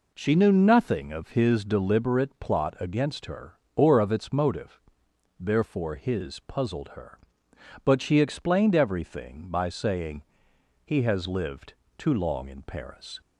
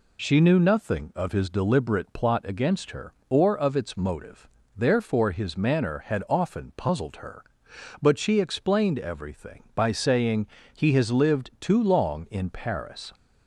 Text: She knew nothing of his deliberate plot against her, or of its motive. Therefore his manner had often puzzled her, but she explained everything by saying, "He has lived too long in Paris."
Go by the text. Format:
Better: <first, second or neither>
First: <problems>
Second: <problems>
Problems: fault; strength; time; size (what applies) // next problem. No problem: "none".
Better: second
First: skips "manner had often"; at 6.3 s // pauses between "lived" and "too"; slight; at 11.7 s; 0.24 s long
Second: none